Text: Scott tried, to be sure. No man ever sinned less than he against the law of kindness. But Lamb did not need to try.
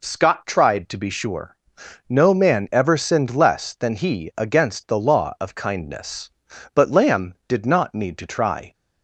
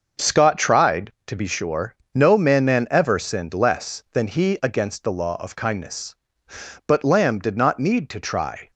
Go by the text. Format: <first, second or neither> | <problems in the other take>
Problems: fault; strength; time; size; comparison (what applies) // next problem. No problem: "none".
first | starts louder than the rest; noticeable; until 1.3 s; 6 dB // says "man" twice; at 2.6 s